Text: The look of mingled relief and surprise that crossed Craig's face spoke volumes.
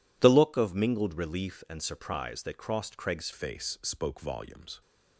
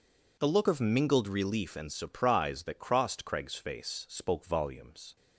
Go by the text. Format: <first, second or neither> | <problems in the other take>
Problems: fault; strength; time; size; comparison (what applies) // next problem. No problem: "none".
second | changes voice at "face"; from 3.3 s on; 1.5 s long